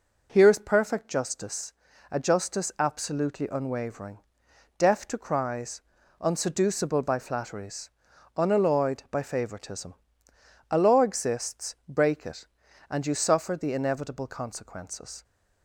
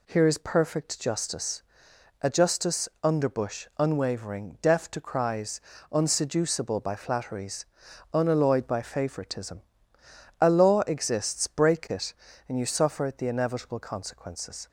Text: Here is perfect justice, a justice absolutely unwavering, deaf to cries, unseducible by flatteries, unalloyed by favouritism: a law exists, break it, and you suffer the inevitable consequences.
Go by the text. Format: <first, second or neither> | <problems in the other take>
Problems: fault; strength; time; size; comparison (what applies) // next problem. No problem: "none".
first | says "underbush" for "absolutely"; at 3.0 s